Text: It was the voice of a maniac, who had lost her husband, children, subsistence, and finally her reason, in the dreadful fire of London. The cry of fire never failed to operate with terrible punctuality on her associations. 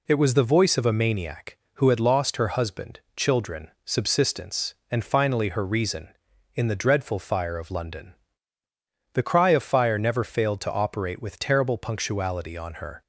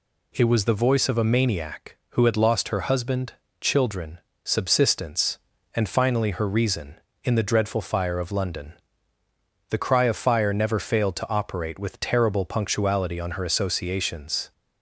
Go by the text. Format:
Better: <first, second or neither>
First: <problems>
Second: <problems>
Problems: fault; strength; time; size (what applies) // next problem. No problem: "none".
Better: second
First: stops before "associations"; at 13.0 s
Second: none